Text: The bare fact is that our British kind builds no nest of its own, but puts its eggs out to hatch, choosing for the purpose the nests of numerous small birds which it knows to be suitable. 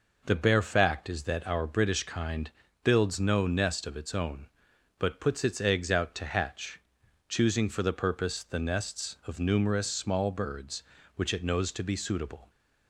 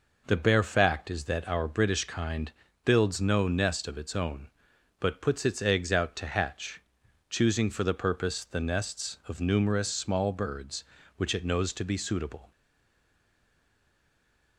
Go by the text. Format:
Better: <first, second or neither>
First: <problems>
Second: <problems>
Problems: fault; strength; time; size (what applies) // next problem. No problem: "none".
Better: first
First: pauses between "kind" and "builds"; slight; at 2.5 s; 0.32 s long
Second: pauses between "kind" and "builds"; slight; at 2.5 s; 0.32 s long // stays silent after the last word; noticeable; from 12.5 s on; 2.0 s long